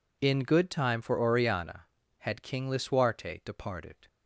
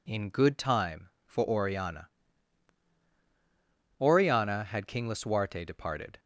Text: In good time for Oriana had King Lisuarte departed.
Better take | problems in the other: first | says "Oriana" twice; at 3.9 s

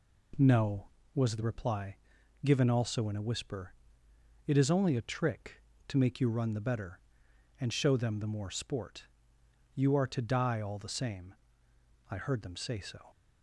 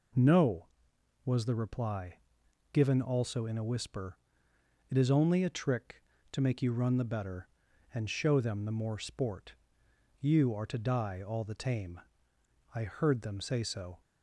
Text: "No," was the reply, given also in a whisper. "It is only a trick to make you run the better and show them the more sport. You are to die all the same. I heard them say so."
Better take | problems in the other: first | says "tame" for "same"; at 11.5 s

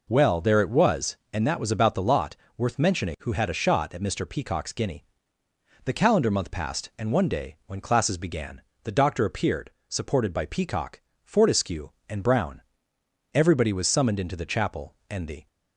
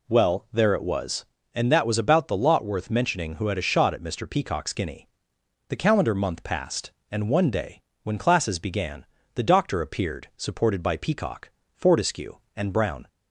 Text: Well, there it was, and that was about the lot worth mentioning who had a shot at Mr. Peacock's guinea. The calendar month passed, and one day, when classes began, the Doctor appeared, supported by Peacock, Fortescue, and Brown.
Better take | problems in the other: second | pauses between "lot" and "worth"; slight; at 2.3 s; 0.22 s long // goes on to say "Everybody was summoned into the chapel and the"; strong; from 13.3 s on; 2.1 s long

